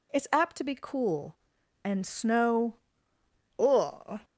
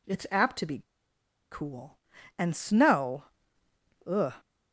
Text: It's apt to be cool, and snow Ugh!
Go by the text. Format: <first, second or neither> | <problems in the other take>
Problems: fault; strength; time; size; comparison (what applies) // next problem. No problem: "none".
first | pauses between "be" and "cool"; noticeable; at 0.7 s; 0.71 s long // pauses between "snow" and "Ugh"; noticeable; at 3.2 s; 0.82 s long; noticeable in the first